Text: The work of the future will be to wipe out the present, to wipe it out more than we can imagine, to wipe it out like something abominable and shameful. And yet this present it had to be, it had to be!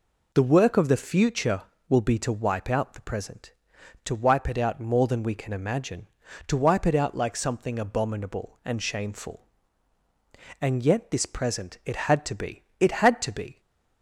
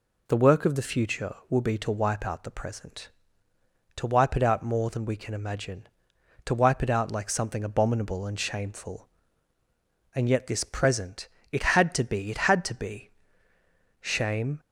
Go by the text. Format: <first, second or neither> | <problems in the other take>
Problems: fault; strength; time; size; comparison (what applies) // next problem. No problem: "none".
first | pauses between "present" and "it"; slight; at 11.2 s; 0.24 s long // goes on to say "Shame"; from 14.0 s on; 0.58 s long